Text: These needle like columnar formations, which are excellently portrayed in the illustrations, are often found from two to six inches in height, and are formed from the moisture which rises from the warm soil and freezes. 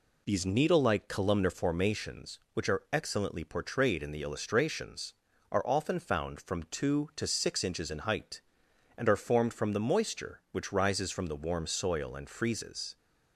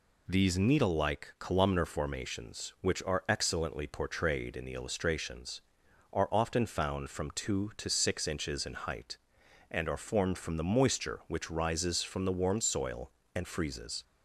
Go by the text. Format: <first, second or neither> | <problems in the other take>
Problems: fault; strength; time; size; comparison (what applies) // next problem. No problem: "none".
neither | none